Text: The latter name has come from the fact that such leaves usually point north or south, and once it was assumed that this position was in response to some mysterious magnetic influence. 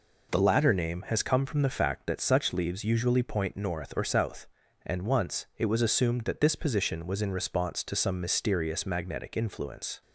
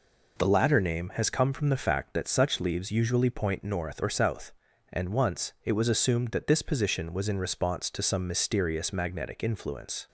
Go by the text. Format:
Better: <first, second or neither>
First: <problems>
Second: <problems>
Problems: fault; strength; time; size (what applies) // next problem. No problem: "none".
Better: neither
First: none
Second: none